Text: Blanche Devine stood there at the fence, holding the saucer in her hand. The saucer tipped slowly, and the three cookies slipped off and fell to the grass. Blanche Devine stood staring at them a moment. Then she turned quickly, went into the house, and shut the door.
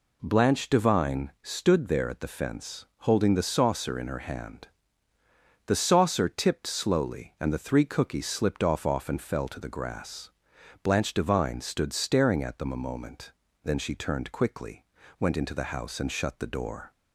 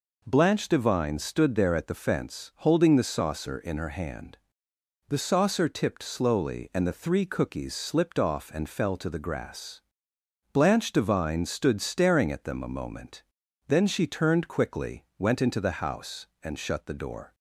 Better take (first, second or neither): second